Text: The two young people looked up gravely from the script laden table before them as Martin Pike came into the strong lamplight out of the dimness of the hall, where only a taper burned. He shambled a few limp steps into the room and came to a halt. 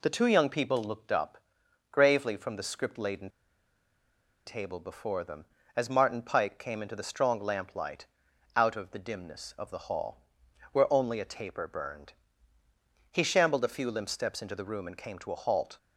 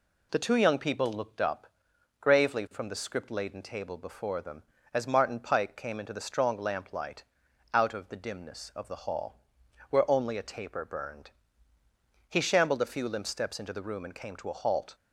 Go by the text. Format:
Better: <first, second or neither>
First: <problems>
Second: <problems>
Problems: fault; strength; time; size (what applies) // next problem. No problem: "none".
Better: second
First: pauses between "up" and "gravely"; noticeable; at 1.3 s; 0.54 s long // pauses between "laden" and "table"; at 3.2 s; 1.1 s long // pauses between "lamplight" and "out"; noticeable; at 8.0 s; 0.50 s long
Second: pauses between "up" and "gravely"; noticeable; at 1.6 s; 0.54 s long // pauses between "lamplight" and "out"; noticeable; at 7.2 s; 0.50 s long